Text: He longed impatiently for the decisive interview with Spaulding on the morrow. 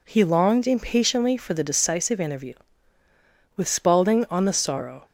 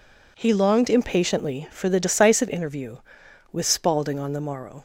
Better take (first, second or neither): second